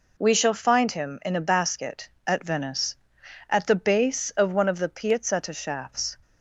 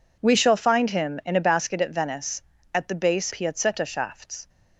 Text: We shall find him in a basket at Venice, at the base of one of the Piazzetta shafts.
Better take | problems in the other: first | skips "of one of the"; at 3.3 s

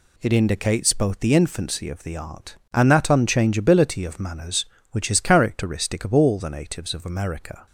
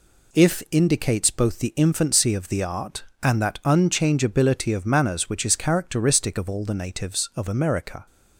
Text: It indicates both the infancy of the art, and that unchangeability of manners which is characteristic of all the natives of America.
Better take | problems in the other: first | says "If" for "It"; at 0.3 s

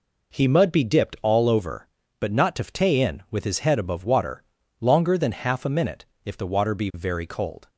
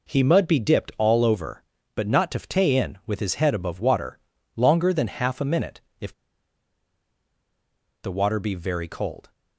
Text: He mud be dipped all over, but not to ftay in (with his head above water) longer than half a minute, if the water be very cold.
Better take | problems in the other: first | pauses between "if" and "the"; strong; at 6.1 s; 1.9 s long

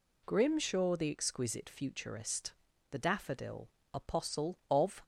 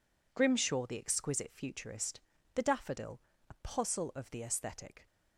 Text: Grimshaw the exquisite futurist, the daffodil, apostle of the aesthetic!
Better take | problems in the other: second | stops before "the aesthetic"; at 5.0 s

